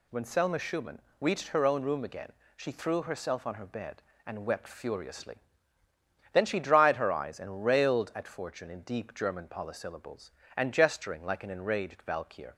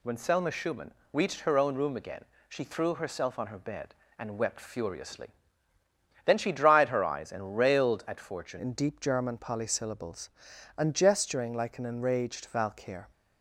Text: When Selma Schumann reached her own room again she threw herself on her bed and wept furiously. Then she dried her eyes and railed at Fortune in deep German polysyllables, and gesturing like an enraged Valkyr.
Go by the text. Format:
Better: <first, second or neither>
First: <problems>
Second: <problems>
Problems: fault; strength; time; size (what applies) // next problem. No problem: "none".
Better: first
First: pauses between "Schumann" and "reached"; slight; at 1.0 s; 0.18 s long // pauses between "again" and "she"; slight; at 2.3 s; 0.24 s long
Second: pauses between "Schumann" and "reached"; slight; at 0.9 s; 0.18 s long // pauses between "again" and "she"; slight; at 2.2 s; 0.24 s long // changes voice at "in"; from 8.5 s on; 4.5 s long